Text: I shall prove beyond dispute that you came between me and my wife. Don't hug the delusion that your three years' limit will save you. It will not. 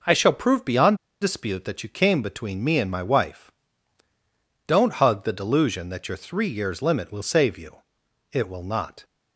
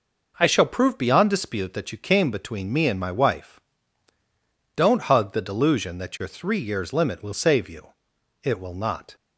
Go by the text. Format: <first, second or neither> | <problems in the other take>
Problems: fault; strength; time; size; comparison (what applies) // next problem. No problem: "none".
second | pauses between "beyond" and "dispute"; slight; at 0.9 s; 0.25 s long